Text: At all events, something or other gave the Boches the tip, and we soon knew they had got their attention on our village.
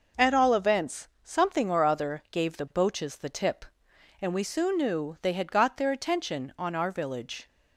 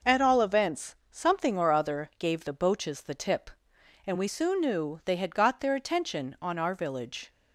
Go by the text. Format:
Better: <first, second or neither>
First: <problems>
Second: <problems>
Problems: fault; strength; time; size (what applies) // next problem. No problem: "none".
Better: neither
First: none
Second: none